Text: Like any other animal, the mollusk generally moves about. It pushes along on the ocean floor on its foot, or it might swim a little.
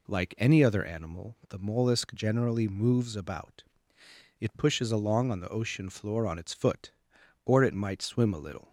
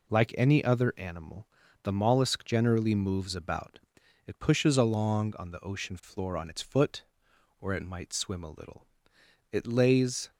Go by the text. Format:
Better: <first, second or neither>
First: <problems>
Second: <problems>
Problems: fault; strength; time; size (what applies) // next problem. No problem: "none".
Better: first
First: none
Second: goes on to say "It lays"; noticeable; from 9.5 s on; 0.78 s long